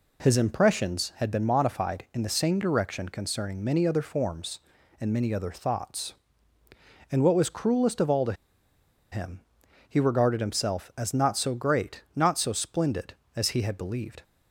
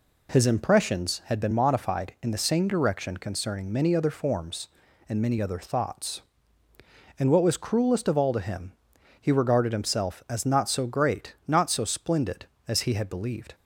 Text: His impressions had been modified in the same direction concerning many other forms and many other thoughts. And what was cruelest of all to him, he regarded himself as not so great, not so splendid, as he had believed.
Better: second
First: pauses between "to" and "him"; noticeable; at 8.3 s; 0.78 s long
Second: none

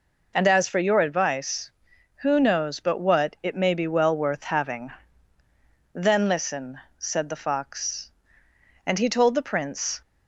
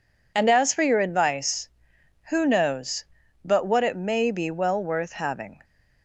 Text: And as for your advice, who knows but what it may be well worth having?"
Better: second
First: goes on to say "Then listen said the fox and he told the Prince"; strong; from 5.9 s on; 4.0 s long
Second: none

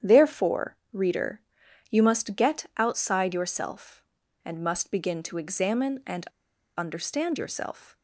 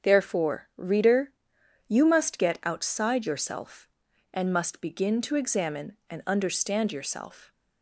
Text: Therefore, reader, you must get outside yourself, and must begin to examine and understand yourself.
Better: second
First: starts louder than the rest; strong; until 1.1 s; 9 dB // pauses between "and" and "understand"; noticeable; at 6.2 s; 0.51 s long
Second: starts louder than the rest; strong; until 1.1 s; 7 dB

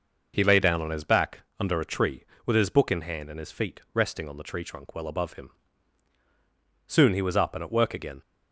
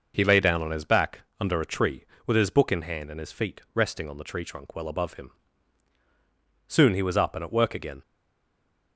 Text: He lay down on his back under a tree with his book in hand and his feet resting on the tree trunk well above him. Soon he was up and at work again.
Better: first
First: pauses between "back" and "under"; slight; at 1.4 s; 0.18 s long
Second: pauses between "back" and "under"; slight; at 1.2 s; 0.18 s long // stays silent after the last word; slight; from 8.0 s on; 0.9 s long

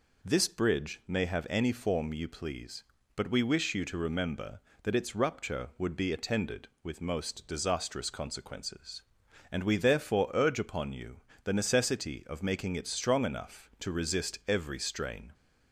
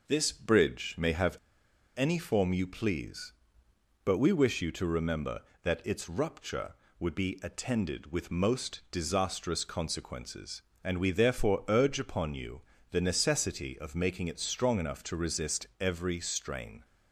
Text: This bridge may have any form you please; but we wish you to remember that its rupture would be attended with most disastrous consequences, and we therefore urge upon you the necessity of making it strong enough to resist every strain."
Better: first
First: pauses between "you" and "the"; slight; at 11.1 s; 0.24 s long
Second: pauses between "have" and "any"; noticeable; at 1.3 s; 0.59 s long // pauses between "you" and "the"; slight; at 12.6 s; 0.30 s long

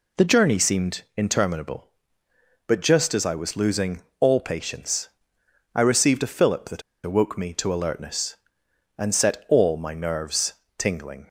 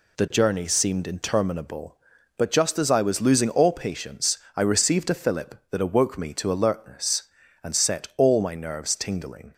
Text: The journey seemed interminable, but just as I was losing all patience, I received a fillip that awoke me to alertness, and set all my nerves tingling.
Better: second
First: pauses between "losing" and "all"; slight; at 4.0 s; 0.18 s long // pauses between "that" and "awoke"; slight; at 6.8 s; 0.23 s long // pauses between "nerves" and "tingling"; slight; at 10.5 s; 0.26 s long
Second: none

